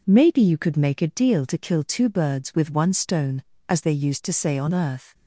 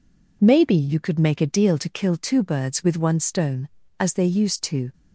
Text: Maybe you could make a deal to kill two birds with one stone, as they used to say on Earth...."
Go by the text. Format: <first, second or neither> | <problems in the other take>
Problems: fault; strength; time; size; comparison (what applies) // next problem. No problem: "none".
first | stops before "say on Earth"; at 4.9 s